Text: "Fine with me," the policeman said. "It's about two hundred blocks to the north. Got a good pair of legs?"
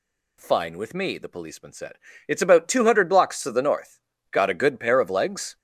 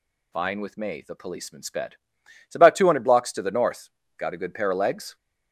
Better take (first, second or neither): first